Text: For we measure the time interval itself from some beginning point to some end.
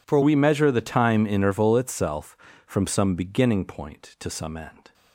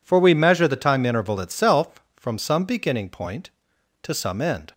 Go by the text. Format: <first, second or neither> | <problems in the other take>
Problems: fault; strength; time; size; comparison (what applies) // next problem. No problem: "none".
second | changes voice at "we"; from 0.2 s on; 4.7 s long